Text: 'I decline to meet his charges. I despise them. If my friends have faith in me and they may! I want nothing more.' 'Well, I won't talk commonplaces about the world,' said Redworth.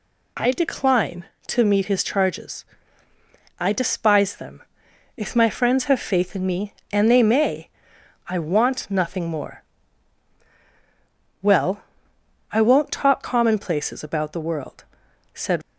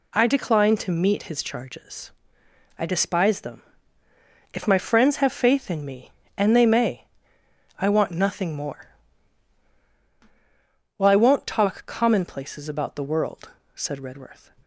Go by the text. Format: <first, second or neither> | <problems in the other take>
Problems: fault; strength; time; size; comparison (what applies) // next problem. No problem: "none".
second | stops before "Redworth"; at 15.6 s